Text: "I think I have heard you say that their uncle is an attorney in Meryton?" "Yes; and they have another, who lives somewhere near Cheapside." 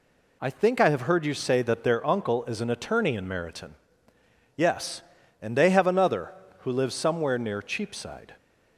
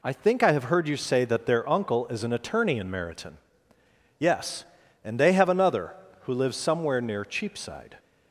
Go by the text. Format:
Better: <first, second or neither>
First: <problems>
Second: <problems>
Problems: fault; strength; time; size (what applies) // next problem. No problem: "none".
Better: neither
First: none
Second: none